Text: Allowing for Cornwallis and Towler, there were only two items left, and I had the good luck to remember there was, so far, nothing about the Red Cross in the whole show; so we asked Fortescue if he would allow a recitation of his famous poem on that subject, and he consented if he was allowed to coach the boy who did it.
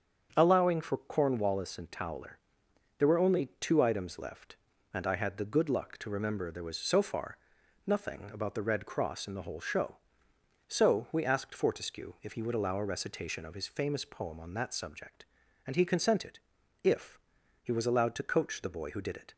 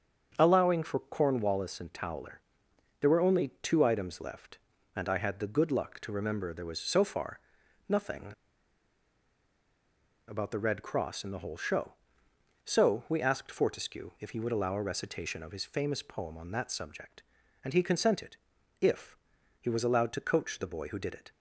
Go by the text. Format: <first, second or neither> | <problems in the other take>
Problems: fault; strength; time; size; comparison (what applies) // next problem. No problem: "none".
first | starts louder than the rest; strong; until 1.3 s; 7 dB; strong in the first // pauses between "nothing" and "about"; strong; at 8.3 s; 1.9 s long // pauses between "consented" and "if"; at 18.3 s; 0.44 s long; also in the first // pauses between "if" and "he"; at 19.1 s; 0.44 s long; also in the first